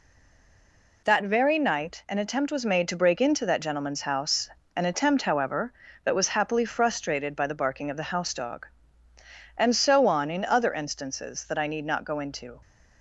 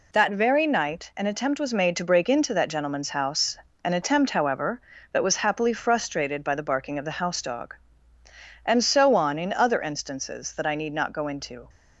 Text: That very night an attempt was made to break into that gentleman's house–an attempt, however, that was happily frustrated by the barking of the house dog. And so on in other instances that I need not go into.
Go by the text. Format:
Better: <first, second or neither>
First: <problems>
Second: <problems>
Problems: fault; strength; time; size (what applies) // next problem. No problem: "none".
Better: second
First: stays silent before the first word; until 1.0 s; 1.0 s long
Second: none